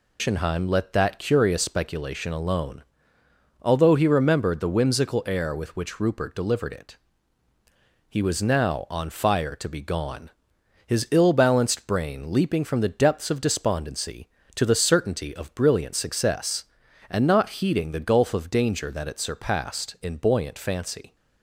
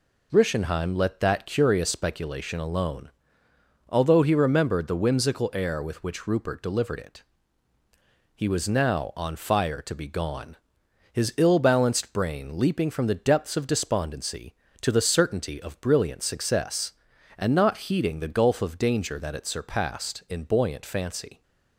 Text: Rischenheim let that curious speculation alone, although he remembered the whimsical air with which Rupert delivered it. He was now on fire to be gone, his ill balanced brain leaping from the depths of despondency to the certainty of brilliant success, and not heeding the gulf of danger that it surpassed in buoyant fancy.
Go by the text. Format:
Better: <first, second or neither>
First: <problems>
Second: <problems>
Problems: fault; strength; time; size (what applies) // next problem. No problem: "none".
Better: second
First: loses the start of "Rischenheim"; at 0.1 s; 150 ms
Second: none